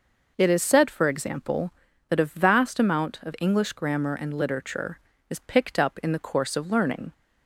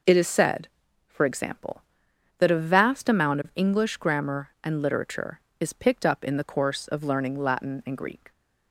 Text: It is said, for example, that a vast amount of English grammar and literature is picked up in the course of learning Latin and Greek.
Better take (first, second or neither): second